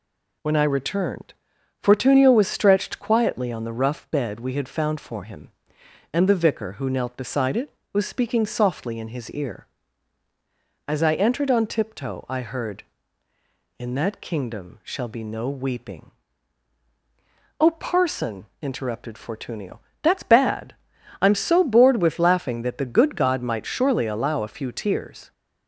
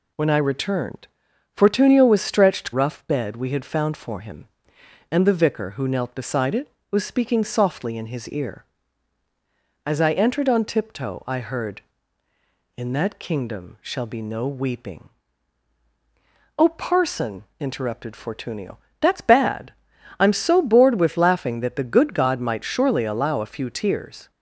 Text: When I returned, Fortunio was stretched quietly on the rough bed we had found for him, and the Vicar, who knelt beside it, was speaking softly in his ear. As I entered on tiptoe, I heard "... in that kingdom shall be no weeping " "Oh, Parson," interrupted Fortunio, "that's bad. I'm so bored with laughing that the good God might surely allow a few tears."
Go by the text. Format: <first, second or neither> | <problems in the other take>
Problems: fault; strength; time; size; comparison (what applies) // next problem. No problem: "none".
first | skips "quietly on the"; at 2.7 s